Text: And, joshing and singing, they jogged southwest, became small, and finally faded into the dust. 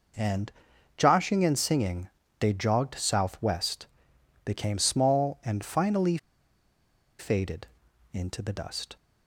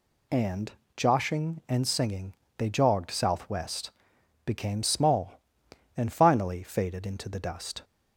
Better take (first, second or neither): second